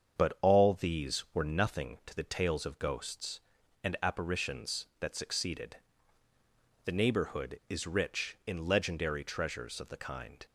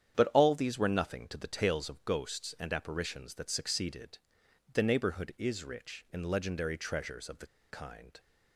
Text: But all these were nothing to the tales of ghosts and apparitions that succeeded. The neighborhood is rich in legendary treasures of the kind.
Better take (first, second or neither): first